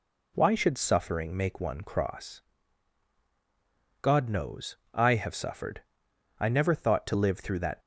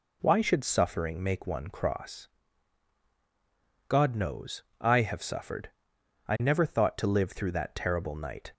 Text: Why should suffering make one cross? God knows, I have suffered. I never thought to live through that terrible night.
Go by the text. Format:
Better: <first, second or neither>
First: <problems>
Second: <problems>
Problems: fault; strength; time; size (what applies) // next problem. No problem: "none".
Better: second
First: stops before "terrible night"; at 7.8 s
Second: none